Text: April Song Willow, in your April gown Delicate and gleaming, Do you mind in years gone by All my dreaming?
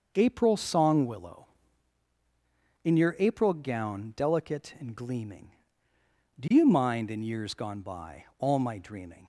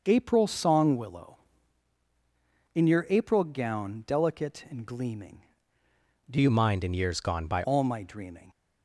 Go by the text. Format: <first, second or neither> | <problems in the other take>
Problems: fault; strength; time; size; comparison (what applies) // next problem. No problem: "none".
first | changes voice from "you" to "by"; from 6.4 to 7.6 s; 1.2 s long